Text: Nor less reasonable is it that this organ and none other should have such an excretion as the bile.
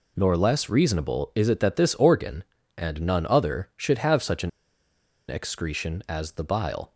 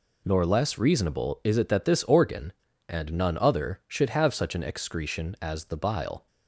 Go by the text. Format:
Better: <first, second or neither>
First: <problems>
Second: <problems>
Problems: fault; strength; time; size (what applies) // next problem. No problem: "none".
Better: second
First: pauses between "an" and "excretion"; noticeable; at 4.4 s; 0.79 s long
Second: none